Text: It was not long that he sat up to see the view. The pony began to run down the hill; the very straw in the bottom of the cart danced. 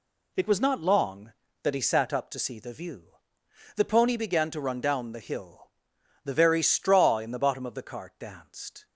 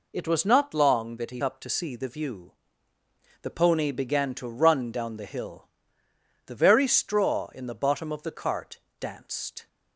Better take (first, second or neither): first